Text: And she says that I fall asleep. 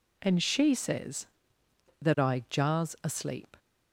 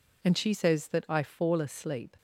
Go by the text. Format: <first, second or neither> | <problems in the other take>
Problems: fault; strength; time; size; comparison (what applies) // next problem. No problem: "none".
second | says "jars" for "fall"; at 2.4 s